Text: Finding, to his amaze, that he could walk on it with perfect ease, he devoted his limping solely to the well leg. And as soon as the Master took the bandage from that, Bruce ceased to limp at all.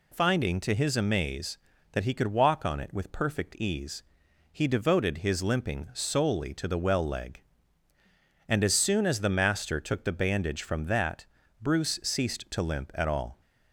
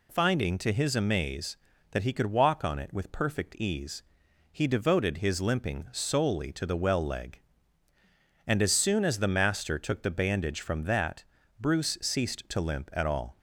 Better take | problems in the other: neither | none

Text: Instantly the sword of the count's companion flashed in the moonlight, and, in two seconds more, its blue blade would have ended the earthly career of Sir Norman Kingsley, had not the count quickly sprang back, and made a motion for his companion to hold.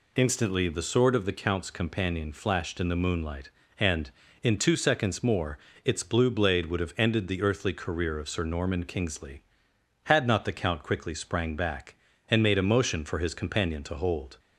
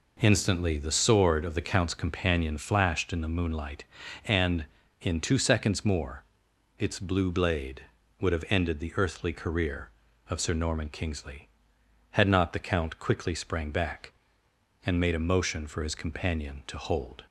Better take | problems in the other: neither | none

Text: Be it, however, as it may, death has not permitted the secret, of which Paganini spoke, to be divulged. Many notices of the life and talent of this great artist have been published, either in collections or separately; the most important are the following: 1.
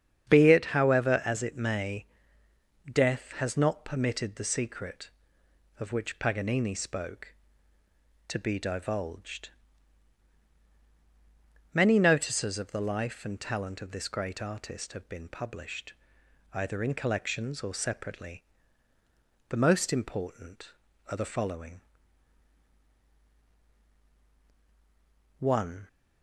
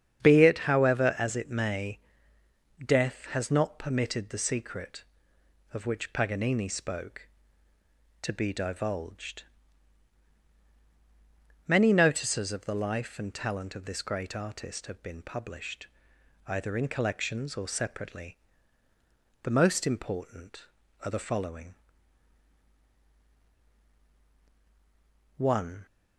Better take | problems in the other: neither | starts louder than the rest; strong; the same in both

